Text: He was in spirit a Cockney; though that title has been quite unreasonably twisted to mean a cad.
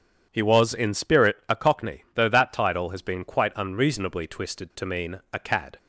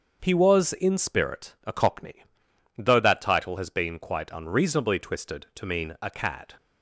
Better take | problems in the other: neither | starts louder than the rest; the same in both

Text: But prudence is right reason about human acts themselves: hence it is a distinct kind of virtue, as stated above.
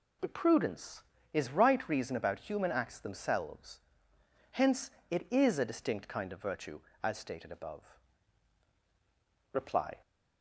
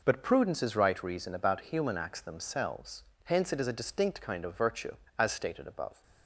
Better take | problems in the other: second | pauses between "hence" and "it"; slight; at 4.9 s; 0.18 s long // goes on to say "Reply"; slight; from 9.5 s on; 0.46 s long

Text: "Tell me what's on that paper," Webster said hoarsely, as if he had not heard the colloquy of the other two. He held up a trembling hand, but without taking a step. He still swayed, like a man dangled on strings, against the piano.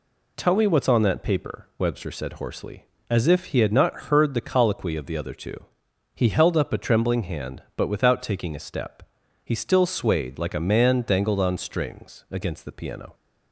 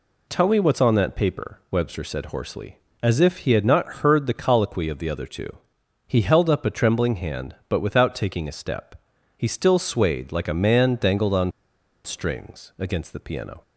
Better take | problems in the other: first | pauses between "on" and "strings"; noticeable; at 11.5 s; 0.54 s long

